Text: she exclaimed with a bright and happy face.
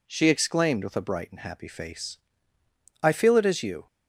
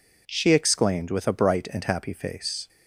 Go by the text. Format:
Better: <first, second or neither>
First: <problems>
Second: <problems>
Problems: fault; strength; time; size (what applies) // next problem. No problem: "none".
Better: second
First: goes on to say "I feel it as you"; noticeable; from 3.0 s on; 0.84 s long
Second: none